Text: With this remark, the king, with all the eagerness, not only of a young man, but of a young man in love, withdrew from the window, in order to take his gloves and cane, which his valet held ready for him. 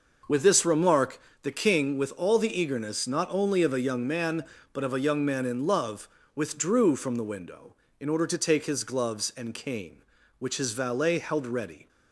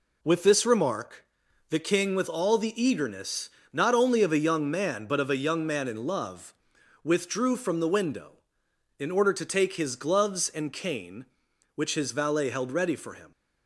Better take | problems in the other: second | stops before "for him"; at 11.8 s

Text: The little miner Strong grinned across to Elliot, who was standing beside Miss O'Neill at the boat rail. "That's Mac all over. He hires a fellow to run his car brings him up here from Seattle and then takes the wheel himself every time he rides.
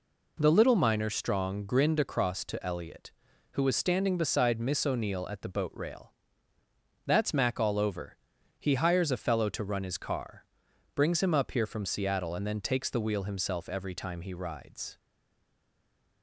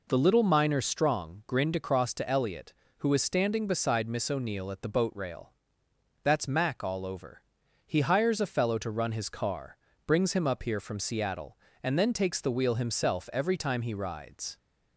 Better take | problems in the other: second | pauses between "car" and "brings"; noticeable; at 10.4 s; 0.50 s long; slight in the second // stays silent after the last word; noticeable; from 14.9 s on; 1.3 s long

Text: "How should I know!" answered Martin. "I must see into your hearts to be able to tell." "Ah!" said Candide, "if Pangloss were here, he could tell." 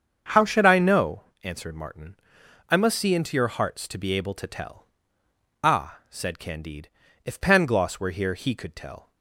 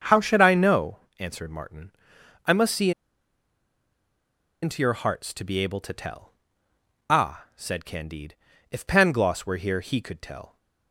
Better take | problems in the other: first | starts louder than the rest; until 1.2 s; 7 dB; also in the first // pauses between "see" and "into"; strong; at 2.9 s; 1.7 s long

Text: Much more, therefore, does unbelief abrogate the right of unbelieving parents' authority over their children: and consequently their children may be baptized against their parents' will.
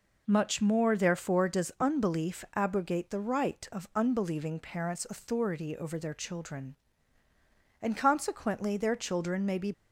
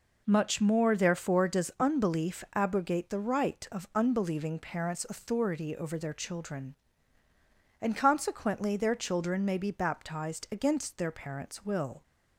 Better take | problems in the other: second | stops before "baptized against their parents will"; at 9.7 s

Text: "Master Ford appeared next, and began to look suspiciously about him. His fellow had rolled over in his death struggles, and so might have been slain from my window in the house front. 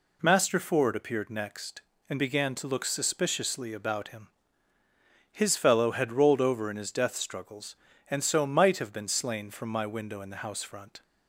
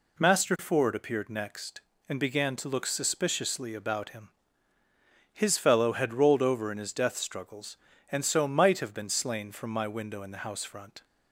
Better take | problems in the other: neither | none

